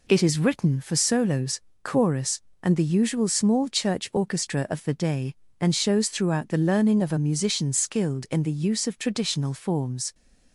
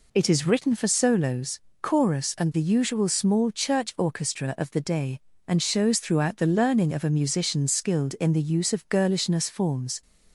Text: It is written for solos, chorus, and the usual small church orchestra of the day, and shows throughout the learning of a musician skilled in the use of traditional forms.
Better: first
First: none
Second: says "girlishness" for "traditional"; at 8.8 s

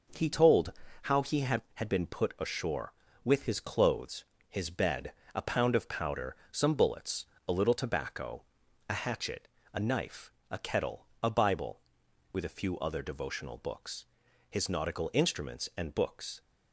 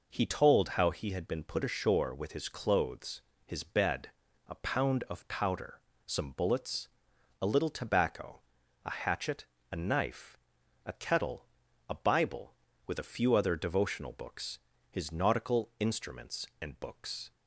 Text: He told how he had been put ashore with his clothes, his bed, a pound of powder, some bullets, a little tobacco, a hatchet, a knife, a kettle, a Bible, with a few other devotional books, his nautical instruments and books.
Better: second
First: pauses between "told" and "how"; slight; at 0.7 s; 0.30 s long // says "had" twice; at 1.7 s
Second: none

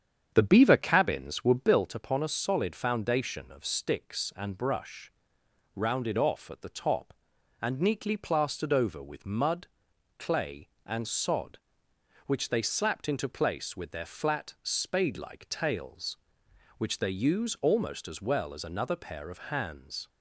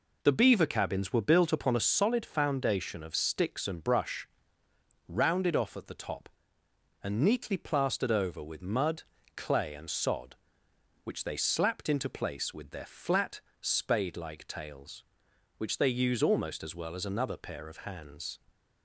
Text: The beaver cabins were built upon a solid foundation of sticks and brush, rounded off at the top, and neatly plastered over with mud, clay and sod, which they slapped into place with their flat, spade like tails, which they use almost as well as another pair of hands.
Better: second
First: starts louder than the rest; strong; until 1.9 s; 8 dB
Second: none

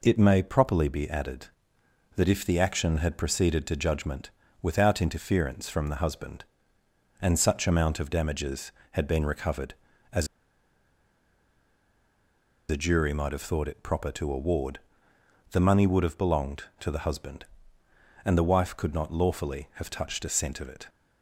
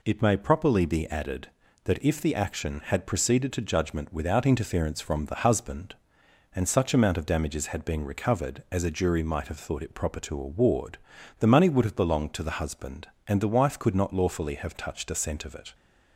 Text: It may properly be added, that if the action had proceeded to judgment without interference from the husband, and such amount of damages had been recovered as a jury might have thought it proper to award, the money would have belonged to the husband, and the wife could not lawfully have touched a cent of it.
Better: second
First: pauses between "judgment" and "without"; slight; at 4.3 s; 0.30 s long // pauses between "as" and "a"; strong; at 10.2 s; 2.4 s long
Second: none

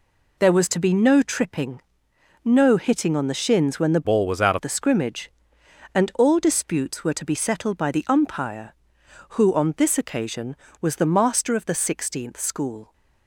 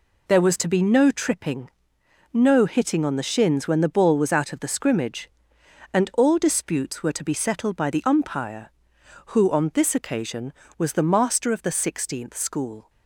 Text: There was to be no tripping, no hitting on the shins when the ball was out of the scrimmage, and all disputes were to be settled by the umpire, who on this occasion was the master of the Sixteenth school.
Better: second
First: changes voice from "ball" to "out"; from 4.0 to 4.5 s; 0.5 s long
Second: none

